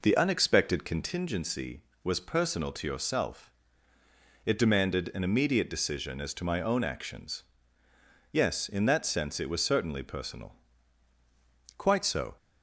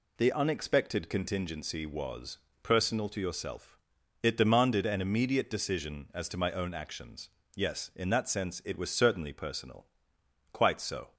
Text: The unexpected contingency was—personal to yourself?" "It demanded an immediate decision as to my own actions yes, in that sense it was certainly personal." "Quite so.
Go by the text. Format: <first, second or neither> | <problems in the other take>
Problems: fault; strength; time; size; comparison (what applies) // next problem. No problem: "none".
second | starts louder than the rest; noticeable; until 1.2 s; 4.5 dB // pauses between "actions" and "yes"; noticeable; at 7.4 s; 0.90 s long; slight in the second